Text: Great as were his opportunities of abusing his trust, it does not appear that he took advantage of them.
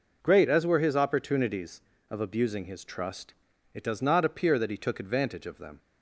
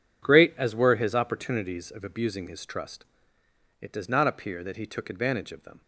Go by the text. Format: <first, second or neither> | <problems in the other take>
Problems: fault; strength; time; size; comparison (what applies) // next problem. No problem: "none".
neither | none